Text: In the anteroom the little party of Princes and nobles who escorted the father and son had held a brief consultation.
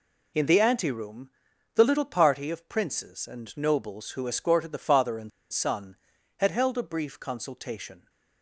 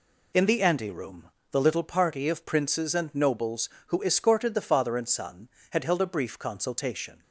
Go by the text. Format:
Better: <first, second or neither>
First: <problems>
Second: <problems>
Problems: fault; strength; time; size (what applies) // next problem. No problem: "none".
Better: second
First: pauses between "anteroom" and "the"; at 1.3 s; 0.42 s long // pauses between "and" and "son"; slight; at 5.3 s; 0.22 s long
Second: pauses between "anteroom" and "the"; slight; at 1.3 s; 0.20 s long